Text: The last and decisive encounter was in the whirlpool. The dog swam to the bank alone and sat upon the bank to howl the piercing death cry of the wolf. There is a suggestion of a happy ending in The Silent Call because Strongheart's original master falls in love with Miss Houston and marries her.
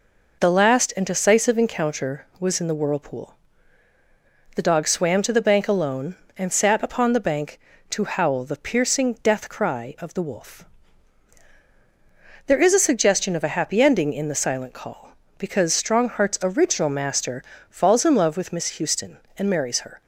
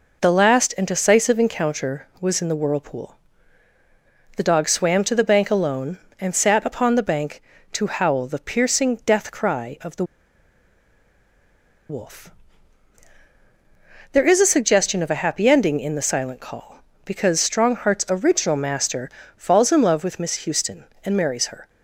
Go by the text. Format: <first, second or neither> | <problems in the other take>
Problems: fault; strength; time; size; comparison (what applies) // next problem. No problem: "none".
first | pauses between "the" and "wolf"; strong; at 10.0 s; 1.8 s long // pauses between "master" and "falls"; slight; at 19.0 s; 0.28 s long; slight in the first